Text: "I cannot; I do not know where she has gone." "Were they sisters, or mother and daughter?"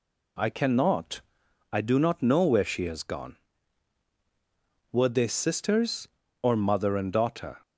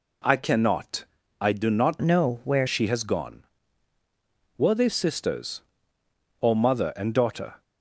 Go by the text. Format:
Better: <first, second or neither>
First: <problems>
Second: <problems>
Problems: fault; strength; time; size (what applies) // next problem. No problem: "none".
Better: first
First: none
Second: changes voice from "know" to "where"; from 2.0 to 2.6 s; 0.6 s long